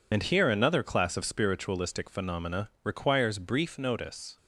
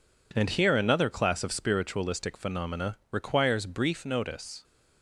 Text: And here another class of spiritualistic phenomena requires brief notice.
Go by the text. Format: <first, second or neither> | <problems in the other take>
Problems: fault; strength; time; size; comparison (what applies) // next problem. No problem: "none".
second | loses the start of "And"; at 0.1 s; 75 ms